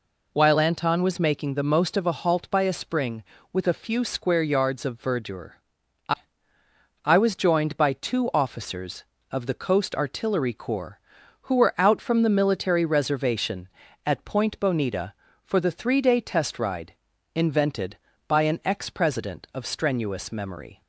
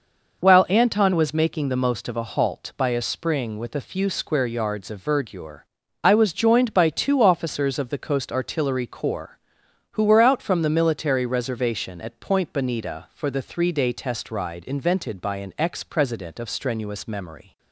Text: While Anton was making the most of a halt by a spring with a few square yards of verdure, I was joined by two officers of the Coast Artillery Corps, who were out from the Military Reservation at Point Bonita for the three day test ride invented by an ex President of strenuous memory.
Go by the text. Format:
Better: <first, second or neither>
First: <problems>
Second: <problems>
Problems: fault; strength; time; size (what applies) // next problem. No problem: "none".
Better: second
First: says "I" twice; at 7.0 s // pauses between "ride" and "invented"; at 16.9 s; 0.40 s long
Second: none